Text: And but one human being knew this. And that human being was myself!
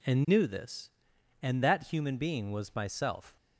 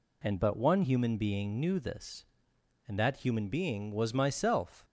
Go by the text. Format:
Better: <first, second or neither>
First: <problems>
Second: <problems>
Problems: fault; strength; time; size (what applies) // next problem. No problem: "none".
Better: second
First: skips "but one human being"; at 0.2 s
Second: none